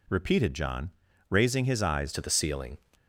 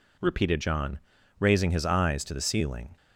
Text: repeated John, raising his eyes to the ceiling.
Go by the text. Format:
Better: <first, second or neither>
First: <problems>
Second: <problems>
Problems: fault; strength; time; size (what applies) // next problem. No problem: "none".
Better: second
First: changes voice at "to"; from 2.1 s on; 0.6 s long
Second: none